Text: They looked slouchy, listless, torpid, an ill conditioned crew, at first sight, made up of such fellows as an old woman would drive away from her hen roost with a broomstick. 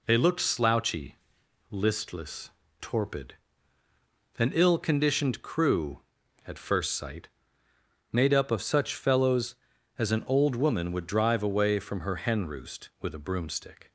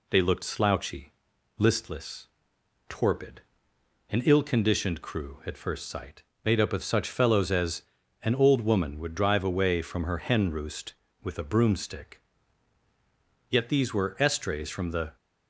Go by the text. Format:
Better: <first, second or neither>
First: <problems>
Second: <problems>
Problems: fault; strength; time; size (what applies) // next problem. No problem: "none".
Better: first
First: none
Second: pauses between "as" and "an"; at 7.8 s; 0.40 s long // goes on to say "Yet these were estrays from the"; from 13.4 s on; 1.6 s long